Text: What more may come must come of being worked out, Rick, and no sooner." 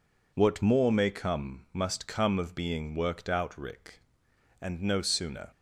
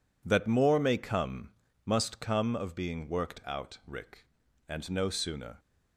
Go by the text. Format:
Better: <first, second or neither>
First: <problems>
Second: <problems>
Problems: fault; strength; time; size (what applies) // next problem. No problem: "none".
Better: first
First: none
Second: says "That" for "What"; at 0.2 s // pauses between "come" and "must"; slight; at 1.4 s; 0.34 s long